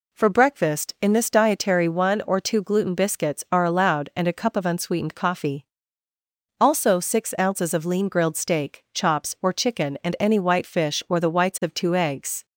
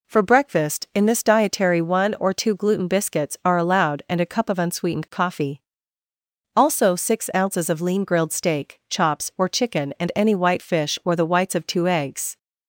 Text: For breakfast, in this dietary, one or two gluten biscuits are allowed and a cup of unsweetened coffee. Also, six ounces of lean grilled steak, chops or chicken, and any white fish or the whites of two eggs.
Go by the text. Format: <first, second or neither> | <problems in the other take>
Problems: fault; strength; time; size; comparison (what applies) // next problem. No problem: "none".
neither | none